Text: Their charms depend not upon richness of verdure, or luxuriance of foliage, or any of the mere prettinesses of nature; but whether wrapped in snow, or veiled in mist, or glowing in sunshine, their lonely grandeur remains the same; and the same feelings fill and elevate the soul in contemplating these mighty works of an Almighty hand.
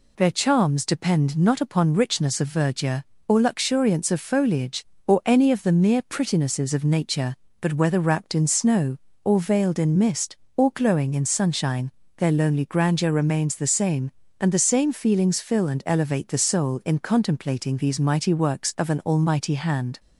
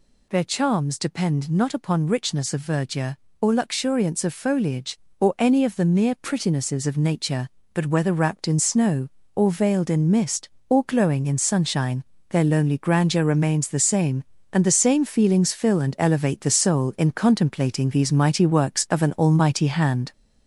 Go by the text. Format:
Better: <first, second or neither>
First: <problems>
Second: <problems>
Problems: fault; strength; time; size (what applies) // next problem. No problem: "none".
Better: first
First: none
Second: gets louder; noticeable; throughout; 4.5 dB